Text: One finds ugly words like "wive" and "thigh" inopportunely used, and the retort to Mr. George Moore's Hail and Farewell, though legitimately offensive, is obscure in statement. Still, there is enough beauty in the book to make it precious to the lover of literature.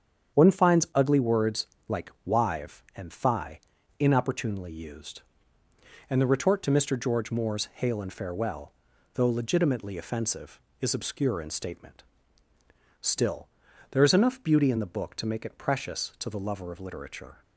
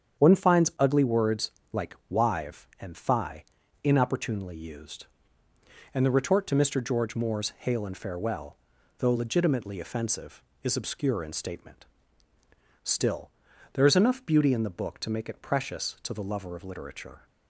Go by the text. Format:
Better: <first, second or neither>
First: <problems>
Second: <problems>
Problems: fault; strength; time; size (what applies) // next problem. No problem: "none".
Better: neither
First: starts louder than the rest; strong; until 1.4 s; 8 dB // pauses between "words" and "like"; slight; at 1.6 s; 0.18 s long // pauses between "like" and "wive"; slight; at 2.1 s; 0.16 s long // pauses between "thigh" and "inopportunely"; at 3.6 s; 0.40 s long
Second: starts louder than the rest; strong; until 1.2 s; 8 dB // pauses between "words" and "like"; slight; at 1.5 s; 0.18 s long // pauses between "like" and "wive"; slight; at 1.9 s; 0.16 s long // pauses between "thigh" and "inopportunely"; at 3.4 s; 0.40 s long